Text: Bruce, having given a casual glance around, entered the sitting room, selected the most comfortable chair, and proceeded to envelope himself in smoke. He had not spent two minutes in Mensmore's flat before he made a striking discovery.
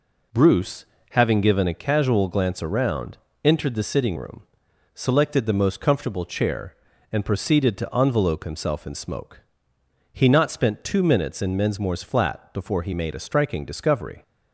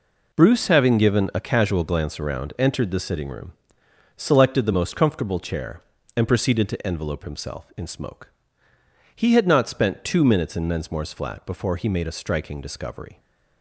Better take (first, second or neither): second